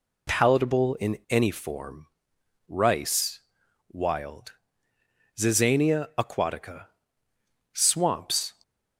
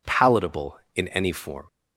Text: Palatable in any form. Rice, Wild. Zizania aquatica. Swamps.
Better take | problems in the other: first | stops before "Rice Wild Zizania aquatica Swamps"; at 1.6 s

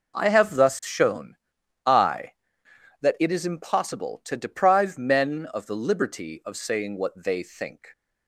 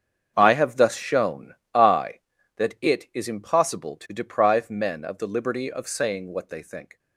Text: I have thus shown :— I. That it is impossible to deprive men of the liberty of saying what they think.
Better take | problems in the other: first | gets quieter; strong; throughout; 14.5 dB

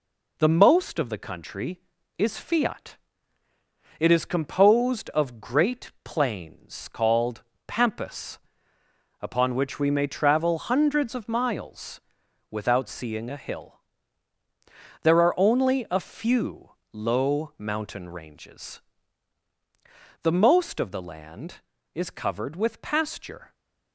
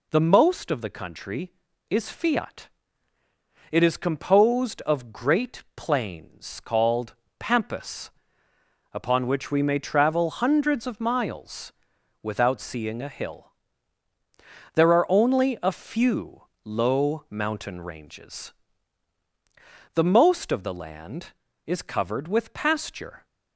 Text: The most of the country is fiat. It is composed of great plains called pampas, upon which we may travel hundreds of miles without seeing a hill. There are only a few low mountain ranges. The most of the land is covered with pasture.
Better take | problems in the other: second | gets quieter; throughout; 4 dB // pauses between "called" and "pampas"; slight; at 7.4 s; 0.24 s long; slight in the second // pauses between "miles" and "without"; noticeable; at 12.0 s; 0.50 s long; noticeable in the second // pauses between "few" and "low"; slight; at 16.7 s; 0.20 s long; slight in the second

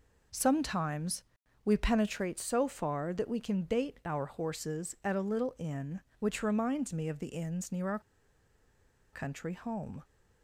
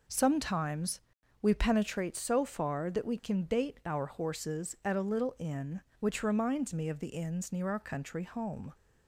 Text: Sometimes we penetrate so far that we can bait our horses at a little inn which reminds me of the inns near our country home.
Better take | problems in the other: second | pauses between "Sometimes" and "we"; at 1.2 s; 0.40 s long; also in the second // pauses between "our" and "country"; at 7.9 s; 1.1 s long

